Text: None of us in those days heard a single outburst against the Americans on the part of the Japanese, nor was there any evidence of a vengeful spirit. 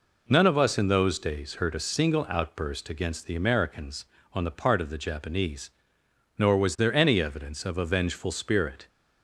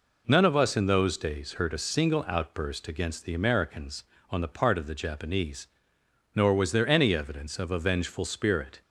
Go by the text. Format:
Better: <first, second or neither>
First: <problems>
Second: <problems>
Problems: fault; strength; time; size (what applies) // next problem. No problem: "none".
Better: neither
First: none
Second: none